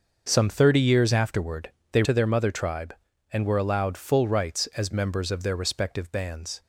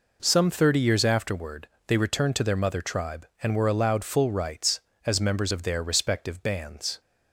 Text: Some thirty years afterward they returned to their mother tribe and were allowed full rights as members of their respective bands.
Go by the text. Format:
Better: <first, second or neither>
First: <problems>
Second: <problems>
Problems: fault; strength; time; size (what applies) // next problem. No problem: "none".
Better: second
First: starts louder than the rest; noticeable; until 1.3 s; 6 dB // pauses between "afterward" and "they"; slight; at 1.7 s; 0.22 s long // skips "returned"; at 2.0 s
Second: pauses between "afterward" and "they"; slight; at 1.6 s; 0.20 s long